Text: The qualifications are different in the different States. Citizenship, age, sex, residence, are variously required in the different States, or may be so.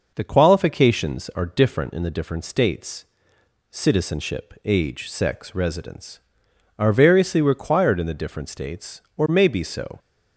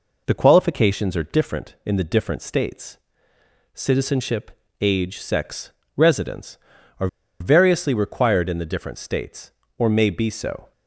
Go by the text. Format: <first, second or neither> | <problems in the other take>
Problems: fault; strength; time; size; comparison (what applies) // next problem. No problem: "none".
first | pauses between "are" and "variously"; slight; at 7.0 s; 0.33 s long